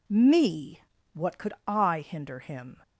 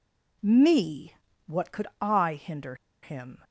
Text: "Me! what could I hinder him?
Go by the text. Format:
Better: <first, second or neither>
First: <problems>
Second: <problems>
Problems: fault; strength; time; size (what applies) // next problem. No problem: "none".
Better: first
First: none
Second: pauses between "hinder" and "him"; slight; at 2.7 s; 0.25 s long